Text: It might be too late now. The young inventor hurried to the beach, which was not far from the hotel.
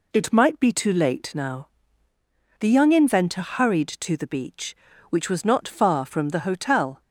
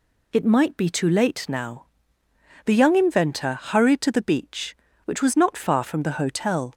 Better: neither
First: none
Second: none

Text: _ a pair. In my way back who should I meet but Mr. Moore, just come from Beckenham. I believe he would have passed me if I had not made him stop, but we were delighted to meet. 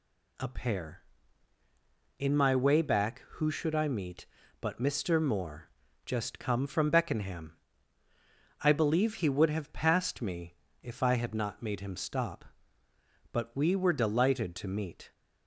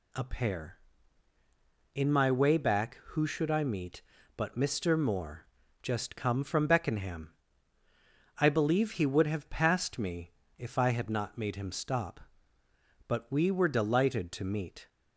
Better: neither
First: pauses between "me" and "if"; slight; at 10.5 s; 0.28 s long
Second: pauses between "me" and "if"; slight; at 10.3 s; 0.26 s long

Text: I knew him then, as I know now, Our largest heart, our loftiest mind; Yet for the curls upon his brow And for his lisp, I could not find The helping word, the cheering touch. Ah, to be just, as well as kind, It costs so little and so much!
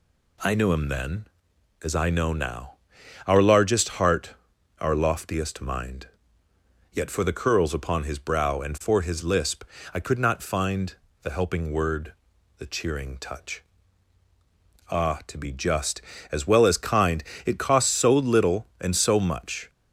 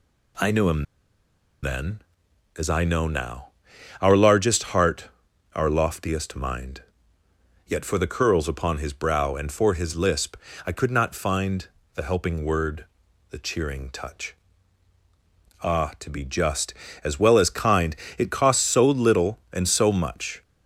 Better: first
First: pauses between "find" and "The"; slight; at 10.9 s; 0.26 s long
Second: pauses between "him" and "then"; noticeable; at 0.8 s; 0.78 s long // pauses between "find" and "The"; slight; at 11.6 s; 0.26 s long

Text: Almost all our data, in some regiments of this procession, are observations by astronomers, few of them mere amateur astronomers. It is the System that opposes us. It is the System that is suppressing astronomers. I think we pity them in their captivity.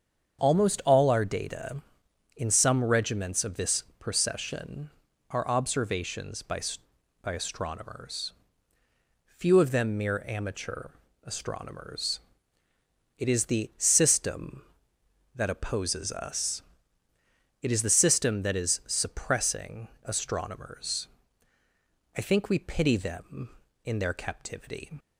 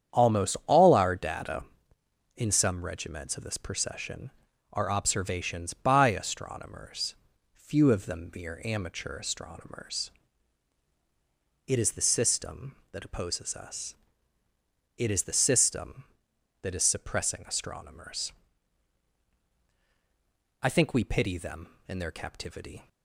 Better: second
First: starts louder than the rest; strong; until 1.4 s; 7.5 dB // pauses between "this" and "procession"; slight; at 3.8 s; 0.16 s long // says "by" twice; at 7.2 s // pauses between "amateur" and "astronomers"; at 10.8 s; 0.38 s long // pauses between "suppressing" and "astronomers"; slight; at 19.8 s; 0.16 s long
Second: starts louder than the rest; strong; until 1.2 s; 8.5 dB

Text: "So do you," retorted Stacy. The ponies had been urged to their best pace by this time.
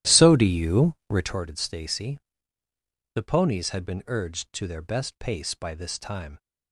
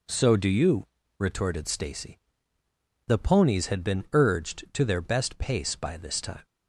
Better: second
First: starts louder than the rest; strong; until 1.4 s; 13 dB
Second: none

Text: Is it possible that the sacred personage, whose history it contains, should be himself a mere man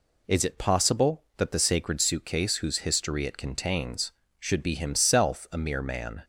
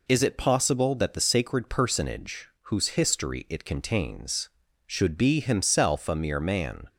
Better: second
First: says "suitcase" for "personage"; at 2.0 s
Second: none

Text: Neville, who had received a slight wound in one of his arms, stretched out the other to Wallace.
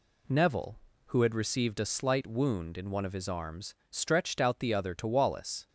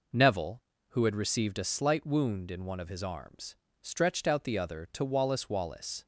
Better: first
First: none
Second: says "Wallace" twice; at 5.4 s

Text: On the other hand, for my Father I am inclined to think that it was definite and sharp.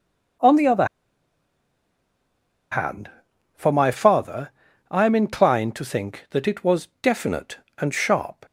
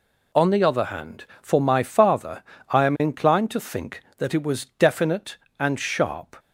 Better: second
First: pauses between "other" and "hand"; strong; at 0.8 s; 1.8 s long // pauses between "Father" and "I"; at 4.5 s; 0.38 s long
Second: pauses between "Father" and "I"; slight; at 2.4 s; 0.28 s long

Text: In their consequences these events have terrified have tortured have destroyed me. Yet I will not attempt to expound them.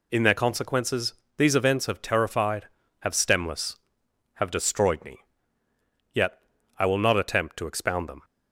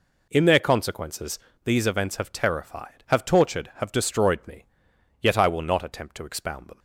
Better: second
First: pauses between "consequences" and "these"; slight; at 1.1 s; 0.22 s long // says "stemless" for "tortured"; at 3.1 s // pauses between "Yet" and "I"; at 6.3 s; 0.40 s long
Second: pauses between "consequences" and "these"; slight; at 1.3 s; 0.28 s long

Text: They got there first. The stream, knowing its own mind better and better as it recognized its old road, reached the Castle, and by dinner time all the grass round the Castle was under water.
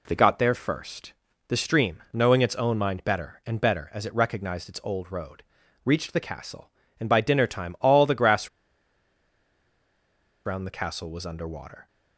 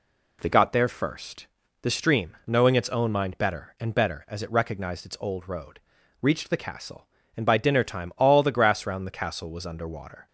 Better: second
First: pauses between "grass" and "round"; strong; at 8.4 s; 1.9 s long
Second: none

